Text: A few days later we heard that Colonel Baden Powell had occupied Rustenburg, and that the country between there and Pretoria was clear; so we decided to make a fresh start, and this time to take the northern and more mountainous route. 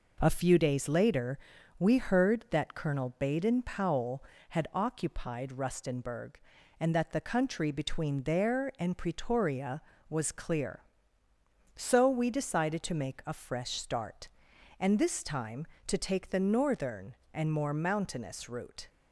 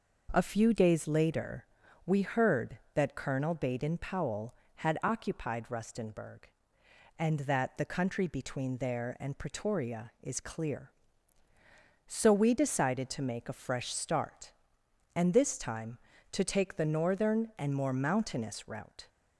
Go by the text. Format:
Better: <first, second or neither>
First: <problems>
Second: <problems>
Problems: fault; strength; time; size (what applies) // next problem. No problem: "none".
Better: first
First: pauses between "later" and "we"; at 1.3 s; 0.40 s long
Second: pauses between "later" and "we"; at 1.6 s; 0.42 s long // says "is" for "was"; at 10.2 s